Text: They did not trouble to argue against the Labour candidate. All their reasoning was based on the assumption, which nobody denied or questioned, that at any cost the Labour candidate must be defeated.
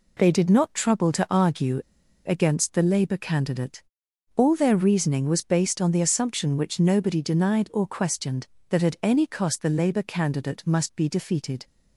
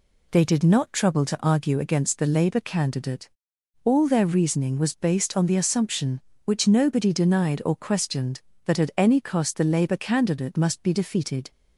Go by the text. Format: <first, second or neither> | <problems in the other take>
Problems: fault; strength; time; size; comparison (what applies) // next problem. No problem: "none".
second | pauses between "argue" and "against"; noticeable; at 1.7 s; 0.46 s long